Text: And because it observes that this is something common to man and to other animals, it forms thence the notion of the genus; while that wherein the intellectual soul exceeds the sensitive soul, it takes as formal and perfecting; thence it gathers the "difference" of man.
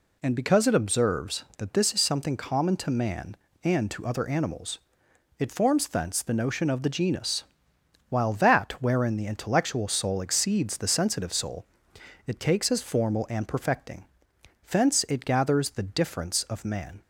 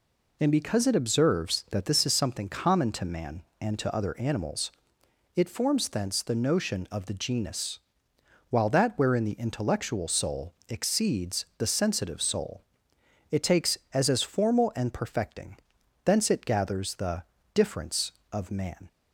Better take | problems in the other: first | pauses between "soul" and "exceeds"; slight; at 10.5 s; 0.16 s long // says "as" twice; at 14.0 s // pauses between "the" and "difference"; slight; at 17.2 s; 0.32 s long

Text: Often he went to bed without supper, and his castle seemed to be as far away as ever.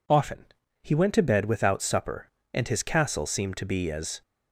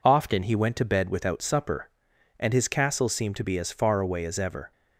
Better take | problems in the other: second | pauses between "Often" and "he"; slight; at 0.4 s; 0.36 s long // stops before "far away as ever"; at 4.2 s

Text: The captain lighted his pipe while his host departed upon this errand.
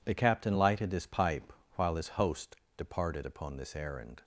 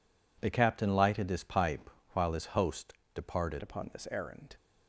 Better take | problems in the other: first | pauses between "pipe" and "while"; slight; at 1.8 s; 0.24 s long; slight in the first // pauses between "host" and "departed"; slight; at 2.9 s; 0.20 s long; slight in the first // changes voice at "upon"; from 3.6 s on; 0.9 s long

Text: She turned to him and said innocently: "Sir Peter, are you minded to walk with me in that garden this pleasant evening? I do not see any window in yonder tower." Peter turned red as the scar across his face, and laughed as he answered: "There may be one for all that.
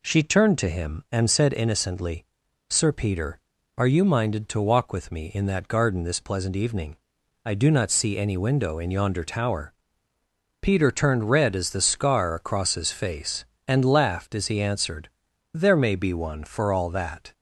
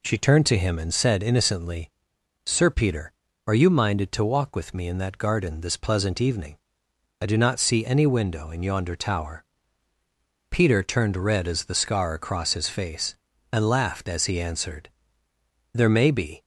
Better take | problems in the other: first | stops before "one for all that"; at 16.4 s

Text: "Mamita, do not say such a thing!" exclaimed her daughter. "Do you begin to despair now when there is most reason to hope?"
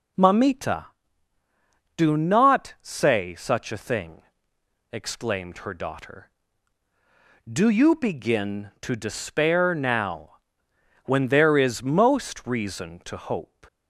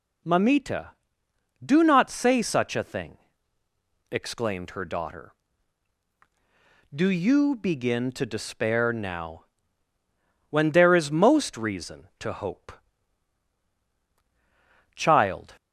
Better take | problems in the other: first | pauses between "now" and "when"; at 9.4 s; 1.0 s long; noticeable in the first // goes on to say "Child"; noticeable; from 14.9 s on; 0.62 s long

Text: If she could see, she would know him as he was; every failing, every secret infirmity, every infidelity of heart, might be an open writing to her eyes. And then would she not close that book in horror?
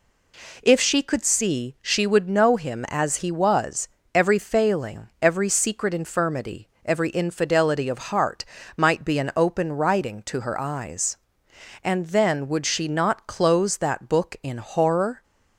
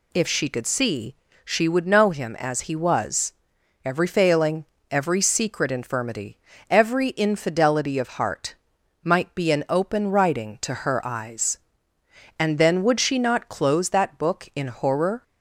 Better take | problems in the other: neither | none

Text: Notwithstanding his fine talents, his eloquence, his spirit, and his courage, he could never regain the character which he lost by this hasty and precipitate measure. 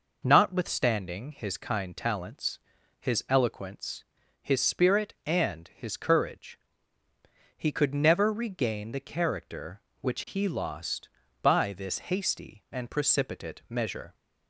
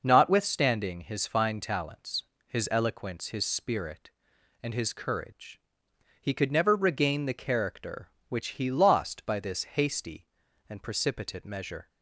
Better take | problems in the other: second | says "kind" for "fine"; at 1.5 s

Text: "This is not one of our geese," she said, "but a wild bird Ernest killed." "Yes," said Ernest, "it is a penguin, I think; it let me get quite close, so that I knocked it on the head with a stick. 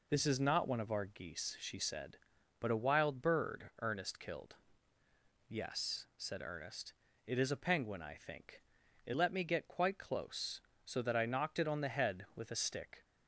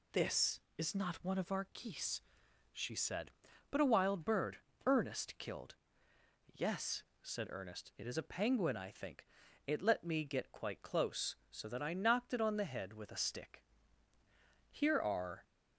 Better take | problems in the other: first | pauses between "bird" and "Ernest"; slight; at 4.5 s; 0.26 s long // goes on to say "Here are"; noticeable; from 14.7 s on; 0.72 s long

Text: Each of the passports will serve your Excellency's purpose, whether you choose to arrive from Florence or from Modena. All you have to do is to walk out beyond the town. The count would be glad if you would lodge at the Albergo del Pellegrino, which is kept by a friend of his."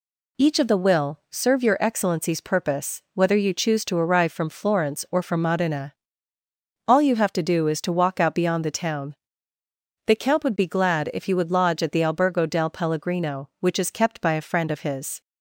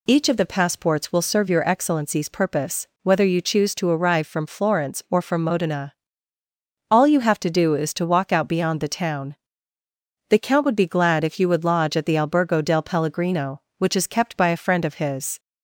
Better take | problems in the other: second | skips "passports"; at 0.7 s

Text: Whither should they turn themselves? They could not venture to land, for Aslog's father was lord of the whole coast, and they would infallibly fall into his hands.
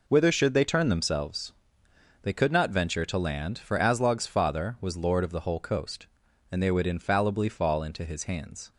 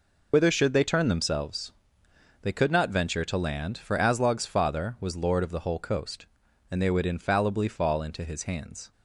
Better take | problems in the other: first | loses the start of "Whither"; at 0.3 s; 60 ms

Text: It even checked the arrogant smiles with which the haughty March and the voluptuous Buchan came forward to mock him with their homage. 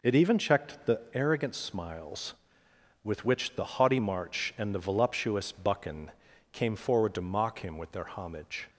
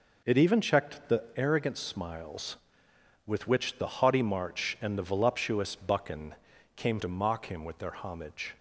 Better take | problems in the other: first | pauses between "Buchan" and "came"; at 6.3 s; 0.42 s long; also in the first // skips "forward"; at 7.0 s

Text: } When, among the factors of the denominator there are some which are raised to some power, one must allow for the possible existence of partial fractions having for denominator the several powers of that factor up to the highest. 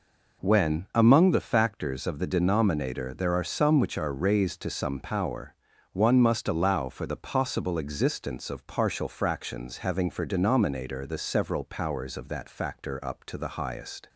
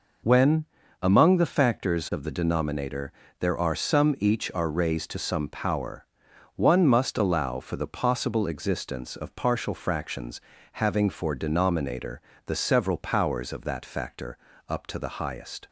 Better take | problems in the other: first | pauses between "denominator" and "there"; slight; at 3.1 s; 0.26 s long // says "each" for "which"; at 4.1 s // pauses between "fractions" and "having"; slight; at 10.3 s; 0.32 s long // pauses between "denominator" and "the"; slight; at 12.1 s; 0.26 s long // pauses between "factor" and "up"; slight; at 14.3 s; 0.32 s long

